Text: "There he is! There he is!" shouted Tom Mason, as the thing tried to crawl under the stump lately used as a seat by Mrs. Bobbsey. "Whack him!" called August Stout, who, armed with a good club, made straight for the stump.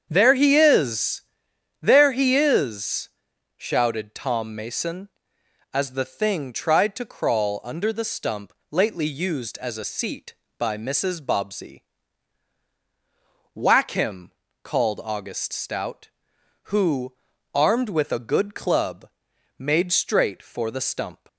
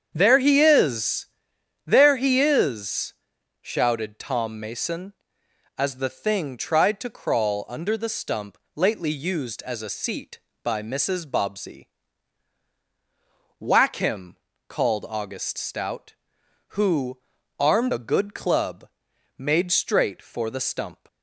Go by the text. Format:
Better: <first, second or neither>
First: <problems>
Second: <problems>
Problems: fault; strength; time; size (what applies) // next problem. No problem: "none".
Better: first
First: starts louder than the rest; strong; until 1.1 s; 8 dB // pauses between "stump" and "lately"; slight; at 8.5 s; 0.16 s long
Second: starts louder than the rest; strong; until 1.1 s; 8 dB // pauses between "stump" and "lately"; slight; at 8.5 s; 0.16 s long // skips "with"; at 17.9 s